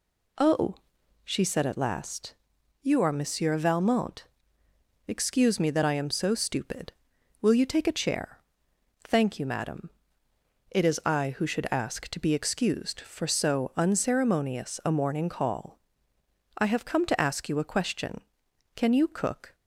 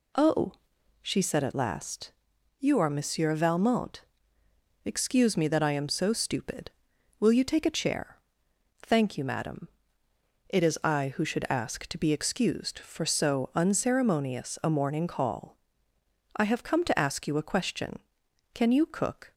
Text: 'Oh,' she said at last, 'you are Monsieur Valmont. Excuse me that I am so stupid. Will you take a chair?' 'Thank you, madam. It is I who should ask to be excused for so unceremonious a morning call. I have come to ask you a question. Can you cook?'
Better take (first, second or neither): neither